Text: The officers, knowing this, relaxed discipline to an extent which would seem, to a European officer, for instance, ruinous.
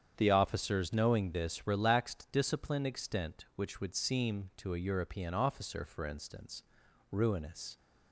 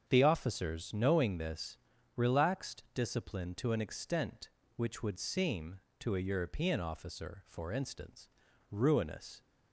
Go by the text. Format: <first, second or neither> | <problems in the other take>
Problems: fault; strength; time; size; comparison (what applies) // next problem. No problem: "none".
second | starts louder than the rest; strong; until 1.1 s; 8.5 dB; strong in the second // skips "to an"; at 2.8 s